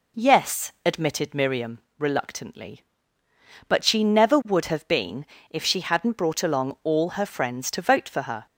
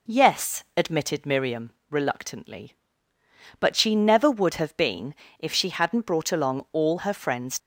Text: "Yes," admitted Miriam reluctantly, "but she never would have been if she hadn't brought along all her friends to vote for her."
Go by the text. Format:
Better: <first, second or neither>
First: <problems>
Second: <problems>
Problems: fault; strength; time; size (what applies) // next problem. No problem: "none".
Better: first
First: pauses between "Miriam" and "reluctantly"; slight; at 1.7 s; 0.20 s long // pauses between "been" and "if"; slight; at 5.2 s; 0.22 s long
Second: pauses between "Miriam" and "reluctantly"; slight; at 1.7 s; 0.20 s long // pauses between "been" and "if"; slight; at 5.1 s; 0.22 s long // stops before "to vote for her"; at 7.5 s